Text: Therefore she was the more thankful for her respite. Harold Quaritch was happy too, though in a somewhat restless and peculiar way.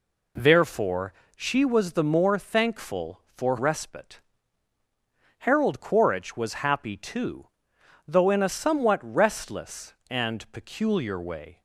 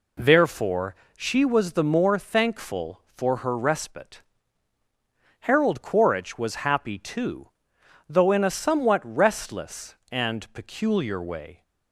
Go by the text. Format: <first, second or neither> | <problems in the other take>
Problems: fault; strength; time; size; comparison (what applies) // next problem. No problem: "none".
second | pauses between "Therefore" and "she"; slight; at 1.1 s; 0.20 s long; slight in the second // skips "her"; at 3.5 s